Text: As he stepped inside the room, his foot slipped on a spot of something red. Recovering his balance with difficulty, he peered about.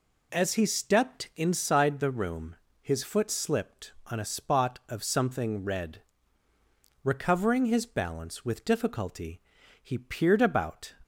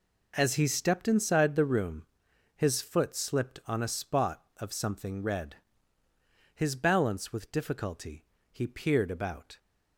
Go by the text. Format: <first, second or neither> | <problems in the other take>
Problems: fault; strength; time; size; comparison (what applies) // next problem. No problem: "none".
first | skips "Recovering"; at 6.0 s